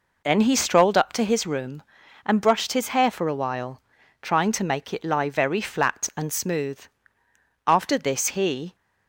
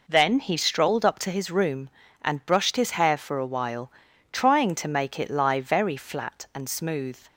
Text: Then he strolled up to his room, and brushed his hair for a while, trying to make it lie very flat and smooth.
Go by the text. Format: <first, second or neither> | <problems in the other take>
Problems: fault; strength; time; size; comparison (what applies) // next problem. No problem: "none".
second | goes on to say "After this he"; noticeable; from 7.6 s on; 1.1 s long